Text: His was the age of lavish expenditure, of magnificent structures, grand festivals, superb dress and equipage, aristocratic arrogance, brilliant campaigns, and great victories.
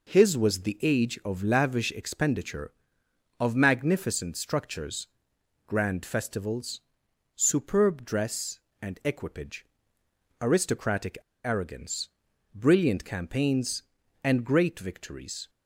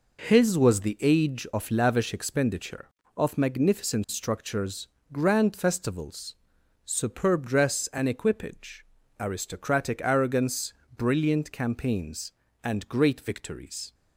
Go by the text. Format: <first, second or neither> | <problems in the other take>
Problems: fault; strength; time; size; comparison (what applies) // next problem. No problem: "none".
second | pauses between "aristocratic" and "arrogance"; slight; at 11.1 s; 0.26 s long